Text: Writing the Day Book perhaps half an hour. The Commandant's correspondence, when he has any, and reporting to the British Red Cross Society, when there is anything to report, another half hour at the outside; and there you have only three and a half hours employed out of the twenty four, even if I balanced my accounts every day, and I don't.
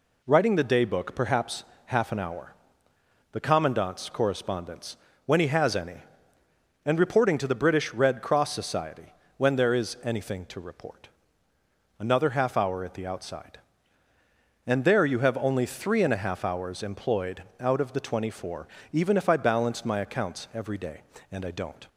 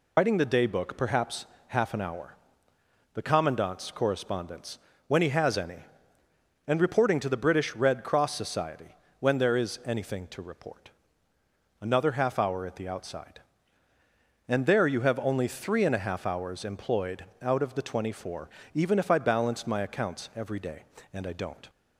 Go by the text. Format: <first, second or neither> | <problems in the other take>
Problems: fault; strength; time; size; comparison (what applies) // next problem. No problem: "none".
first | loses the start of "Writing"; at 0.1 s; 110 ms // pauses between "perhaps" and "half"; slight; at 1.4 s; 0.22 s long; slight in the first // pauses between "employed" and "out"; slight; at 17.2 s; 0.18 s long; slight in the first